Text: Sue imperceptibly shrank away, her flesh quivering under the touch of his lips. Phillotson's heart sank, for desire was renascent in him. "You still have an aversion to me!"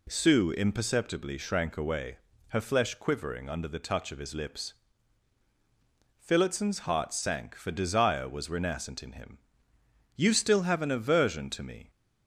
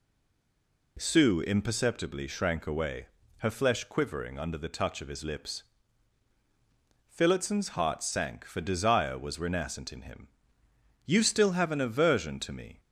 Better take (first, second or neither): first